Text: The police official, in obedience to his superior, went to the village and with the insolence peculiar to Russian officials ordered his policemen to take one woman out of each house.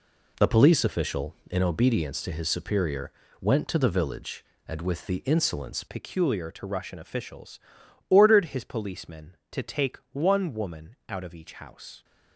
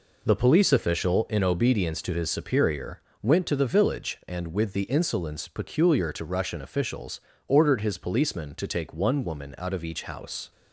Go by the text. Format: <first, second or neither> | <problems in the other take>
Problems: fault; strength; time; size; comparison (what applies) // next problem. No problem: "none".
second | changes voice at "peculiar"; from 5.8 s on; 6.2 s long // pauses between "officials" and "ordered"; noticeable; at 7.5 s; 0.50 s long; slight in the second